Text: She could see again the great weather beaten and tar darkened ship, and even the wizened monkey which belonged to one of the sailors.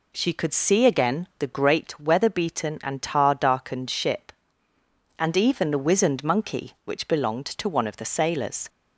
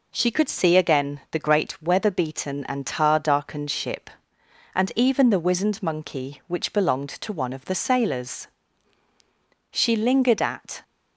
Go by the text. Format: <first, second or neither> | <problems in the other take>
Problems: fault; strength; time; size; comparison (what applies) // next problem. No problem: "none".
first | goes on to say "She lingered at"; noticeable; from 9.7 s on; 1.1 s long